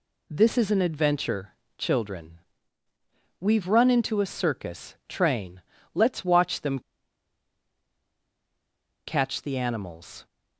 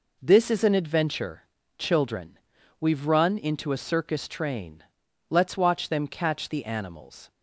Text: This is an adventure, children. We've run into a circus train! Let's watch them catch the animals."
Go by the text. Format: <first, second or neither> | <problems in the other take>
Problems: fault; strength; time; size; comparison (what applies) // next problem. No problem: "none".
second | pauses between "them" and "catch"; strong; at 6.7 s; 2.2 s long